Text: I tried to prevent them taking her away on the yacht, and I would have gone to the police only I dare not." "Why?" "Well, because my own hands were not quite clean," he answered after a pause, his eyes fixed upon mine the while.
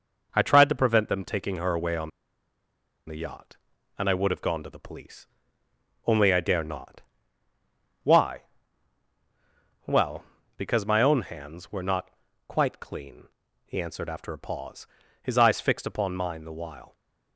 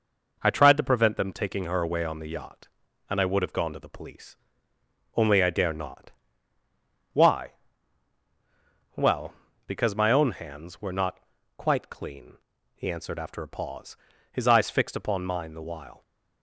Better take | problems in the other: second | pauses between "on" and "the"; at 2.1 s; 0.98 s long // pauses between "police" and "only"; noticeable; at 5.2 s; 0.82 s long; noticeable in the second // pauses between "not" and "quite"; at 12.0 s; 0.38 s long; also in the second

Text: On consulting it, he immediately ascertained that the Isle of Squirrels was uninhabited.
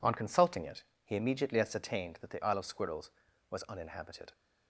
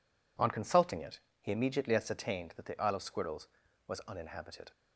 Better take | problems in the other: neither | none

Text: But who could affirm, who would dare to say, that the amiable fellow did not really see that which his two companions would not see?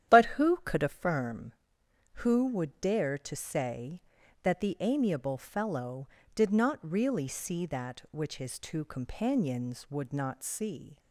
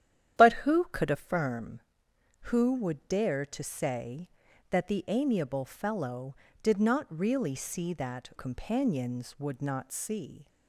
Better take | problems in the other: first | starts louder than the rest; strong; until 1.4 s; 10.5 dB; strong in the first // skips "which his two"; at 8.3 s

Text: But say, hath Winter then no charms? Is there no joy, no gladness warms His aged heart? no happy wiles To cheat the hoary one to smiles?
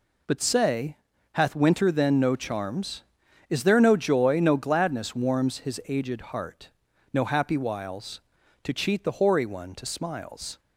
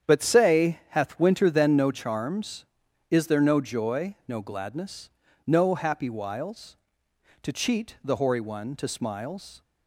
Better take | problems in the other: first | starts louder than the rest; strong; until 1.1 s; 8.5 dB // skips "warms His aged heart"; at 5.2 s

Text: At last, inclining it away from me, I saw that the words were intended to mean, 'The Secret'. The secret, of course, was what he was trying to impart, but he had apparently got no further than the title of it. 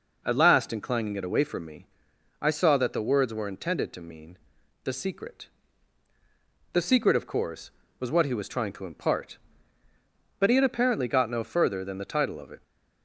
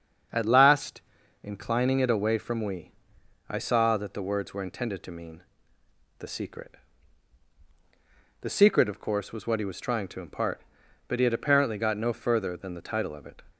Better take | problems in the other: first | starts louder than the rest; until 1.7 s; 7 dB // says "we" for "me"; at 2.6 s

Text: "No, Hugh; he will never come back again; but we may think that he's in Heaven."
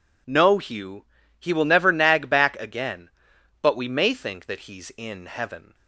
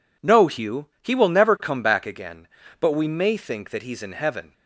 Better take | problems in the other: second | says "nag" for "come"; at 1.9 s

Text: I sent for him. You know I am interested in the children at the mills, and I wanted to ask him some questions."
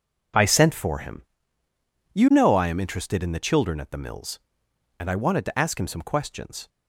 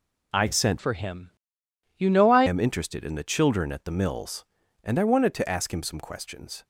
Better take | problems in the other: first | changes voice from "for" to "I"; from 0.7 to 2.4 s; 1.7 s long

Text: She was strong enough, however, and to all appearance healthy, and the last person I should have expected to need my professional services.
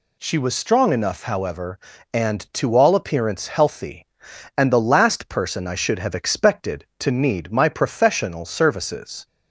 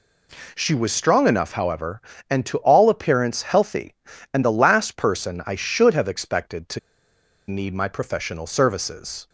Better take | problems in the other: first | pauses between "to" and "need"; noticeable; at 6.7 s; 0.69 s long

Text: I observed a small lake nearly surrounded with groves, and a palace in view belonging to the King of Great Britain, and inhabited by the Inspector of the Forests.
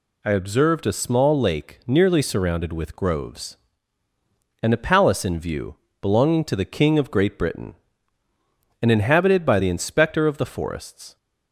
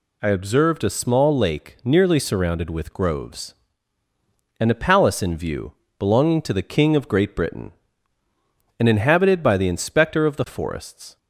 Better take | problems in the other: neither | pauses between "view" and "belonging"; slight; the same in both

